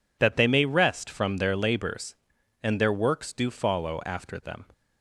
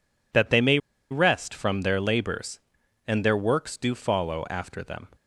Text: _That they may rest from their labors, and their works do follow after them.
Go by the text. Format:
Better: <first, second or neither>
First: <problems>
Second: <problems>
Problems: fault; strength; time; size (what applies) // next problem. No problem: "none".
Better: first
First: none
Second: pauses between "may" and "rest"; slight; at 0.7 s; 0.33 s long